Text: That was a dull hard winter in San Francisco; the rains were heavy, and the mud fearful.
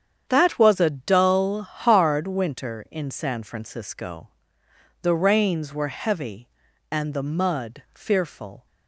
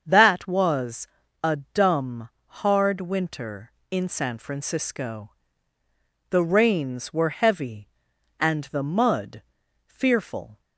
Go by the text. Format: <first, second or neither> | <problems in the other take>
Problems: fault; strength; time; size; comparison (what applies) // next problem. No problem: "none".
first | starts louder than the rest; until 1.0 s; 7 dB; strong in the first // pauses between "was" and "a"; at 1.0 s; 0.38 s long // says "dumb" for "dull"; at 1.7 s // pauses between "mud" and "fearful"; at 9.4 s; 0.44 s long